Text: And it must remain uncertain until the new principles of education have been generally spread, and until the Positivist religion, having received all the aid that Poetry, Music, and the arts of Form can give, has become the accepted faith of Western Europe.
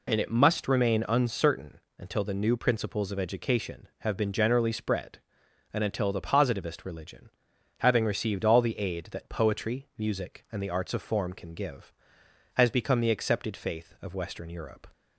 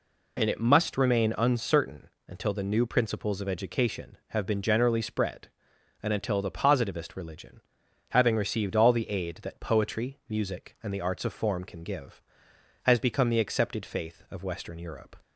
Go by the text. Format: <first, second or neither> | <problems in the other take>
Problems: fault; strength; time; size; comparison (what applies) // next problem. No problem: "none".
neither | pauses between "uncertain" and "until"; slight; the same in both